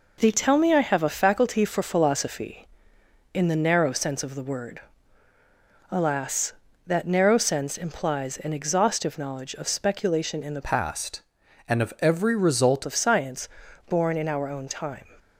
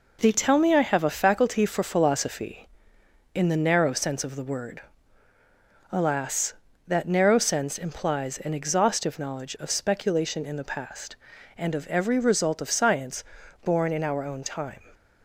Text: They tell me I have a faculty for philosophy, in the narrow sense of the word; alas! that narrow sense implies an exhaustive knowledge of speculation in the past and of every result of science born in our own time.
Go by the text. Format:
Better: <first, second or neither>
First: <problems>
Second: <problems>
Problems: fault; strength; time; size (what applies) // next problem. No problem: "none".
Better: second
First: changes voice from "past" to "result"; from 10.6 to 12.8 s; 2.2 s long // pauses between "science" and "born"; at 13.4 s; 0.40 s long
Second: pauses between "science" and "born"; at 13.2 s; 0.40 s long